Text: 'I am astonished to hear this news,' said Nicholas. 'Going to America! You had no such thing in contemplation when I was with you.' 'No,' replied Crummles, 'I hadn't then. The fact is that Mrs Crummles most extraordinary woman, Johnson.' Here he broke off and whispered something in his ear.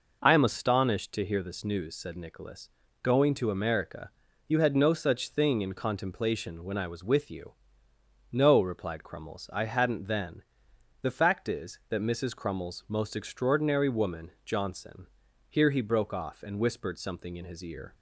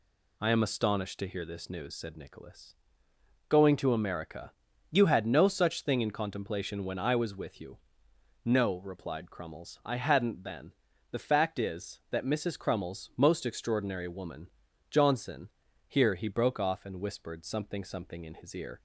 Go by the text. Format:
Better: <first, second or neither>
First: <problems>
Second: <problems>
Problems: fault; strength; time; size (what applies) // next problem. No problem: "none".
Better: first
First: none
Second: says "something" twice; at 17.8 s